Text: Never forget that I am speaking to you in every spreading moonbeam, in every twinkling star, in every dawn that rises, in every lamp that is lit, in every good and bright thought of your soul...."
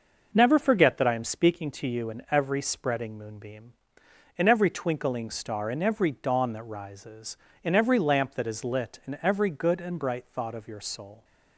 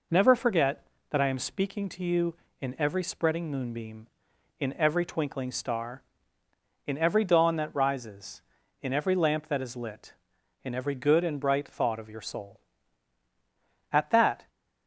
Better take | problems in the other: first | goes on to say "At that"; from 13.9 s on; 0.58 s long

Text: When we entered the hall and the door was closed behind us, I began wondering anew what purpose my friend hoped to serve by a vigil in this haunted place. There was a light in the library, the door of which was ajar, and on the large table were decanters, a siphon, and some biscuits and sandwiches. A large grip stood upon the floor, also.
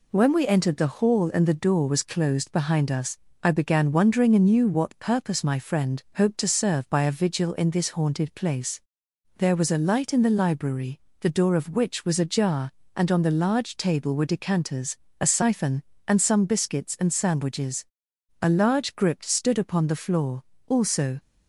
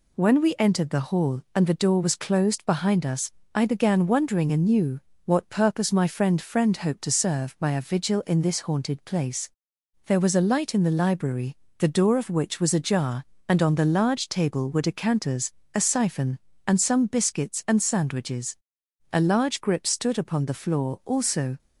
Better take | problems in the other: first | pauses between "anew" and "what"; slight; at 4.9 s; 0.26 s long // says "friend" twice; at 6.3 s

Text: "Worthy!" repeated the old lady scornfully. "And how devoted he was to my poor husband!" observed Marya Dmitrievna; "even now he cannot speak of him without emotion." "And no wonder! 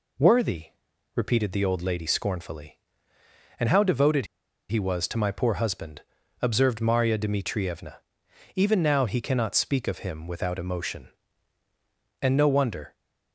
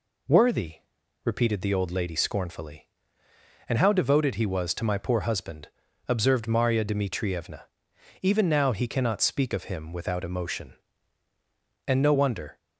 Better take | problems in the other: second | pauses between "devoted" and "he"; at 4.2 s; 0.44 s long

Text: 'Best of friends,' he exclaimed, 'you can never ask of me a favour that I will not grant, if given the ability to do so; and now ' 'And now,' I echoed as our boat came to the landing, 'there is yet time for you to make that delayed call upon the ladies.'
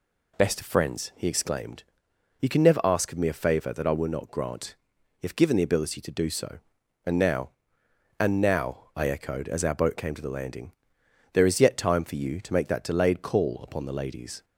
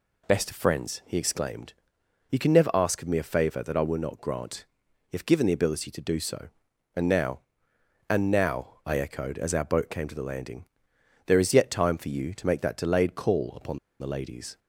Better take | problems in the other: first | pauses between "upon" and "the"; slight; at 13.7 s; 0.21 s long

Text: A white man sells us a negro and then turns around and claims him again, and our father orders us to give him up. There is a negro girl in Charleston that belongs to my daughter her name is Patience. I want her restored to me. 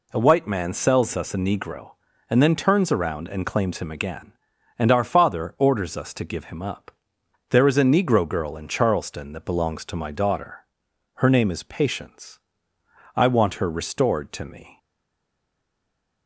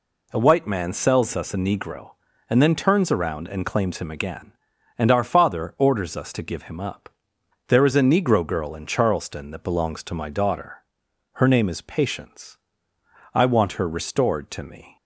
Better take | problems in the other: second | pauses between "daughter" and "her"; noticeable; at 10.6 s; 0.52 s long; noticeable in the second // stays silent after the last word; noticeable; from 14.7 s on; 1.5 s long

